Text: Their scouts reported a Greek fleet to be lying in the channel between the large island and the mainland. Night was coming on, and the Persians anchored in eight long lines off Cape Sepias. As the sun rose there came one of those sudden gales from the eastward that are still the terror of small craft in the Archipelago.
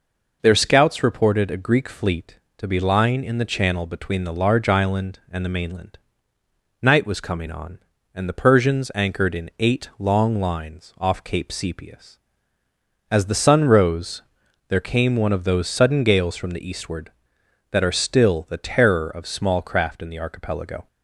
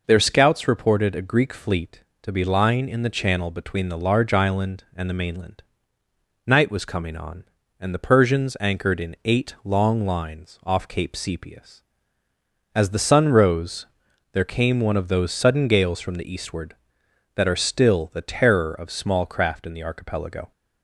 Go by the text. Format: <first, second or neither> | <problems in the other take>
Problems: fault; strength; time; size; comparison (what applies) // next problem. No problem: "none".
neither | pauses between "rose" and "there"; noticeable; the same in both